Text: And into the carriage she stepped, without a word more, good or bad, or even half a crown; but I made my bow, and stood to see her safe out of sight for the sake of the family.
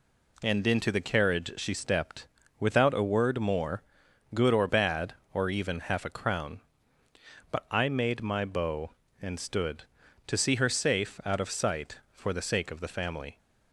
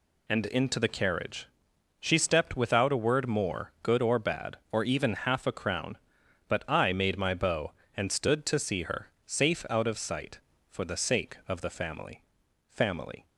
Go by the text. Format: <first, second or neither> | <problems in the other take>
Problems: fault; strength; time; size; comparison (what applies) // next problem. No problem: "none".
first | pauses between "carriage" and "she"; noticeable; at 1.4 s; 0.54 s long // says "family" twice; at 12.6 s